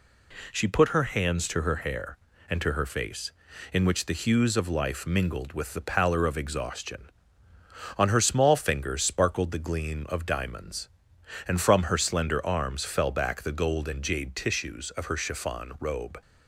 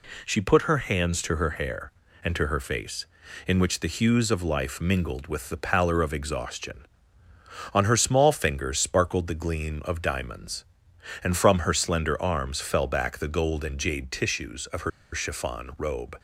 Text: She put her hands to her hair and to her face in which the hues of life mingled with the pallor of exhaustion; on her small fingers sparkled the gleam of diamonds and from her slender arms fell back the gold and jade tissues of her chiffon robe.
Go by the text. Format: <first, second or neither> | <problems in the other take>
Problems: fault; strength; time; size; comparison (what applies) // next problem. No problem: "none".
first | pauses between "her" and "chiffon"; slight; at 14.9 s; 0.24 s long